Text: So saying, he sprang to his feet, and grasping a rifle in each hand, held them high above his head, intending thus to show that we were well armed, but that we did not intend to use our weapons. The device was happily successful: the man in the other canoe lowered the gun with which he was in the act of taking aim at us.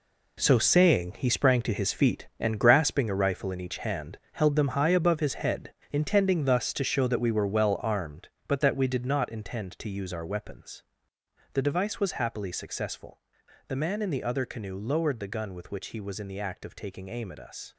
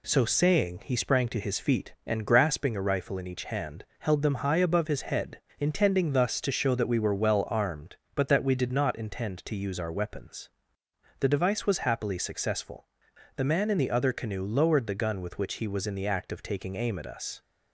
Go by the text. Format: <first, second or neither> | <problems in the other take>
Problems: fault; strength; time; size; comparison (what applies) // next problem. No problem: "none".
second | gets quieter; strong; throughout; 10 dB